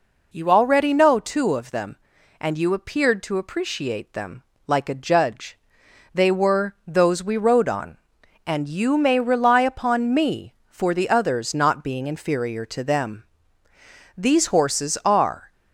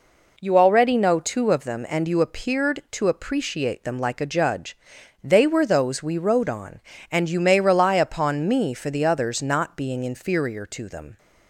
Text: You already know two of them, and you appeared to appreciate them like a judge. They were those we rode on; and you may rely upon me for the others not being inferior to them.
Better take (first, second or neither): second